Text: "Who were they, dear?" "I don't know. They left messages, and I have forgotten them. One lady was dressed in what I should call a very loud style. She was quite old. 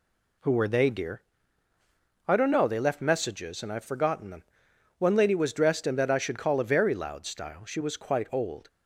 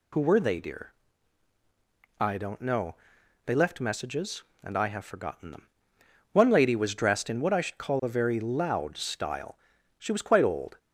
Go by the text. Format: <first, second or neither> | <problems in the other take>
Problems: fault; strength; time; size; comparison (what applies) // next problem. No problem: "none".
second | says "that" for "what"; at 5.9 s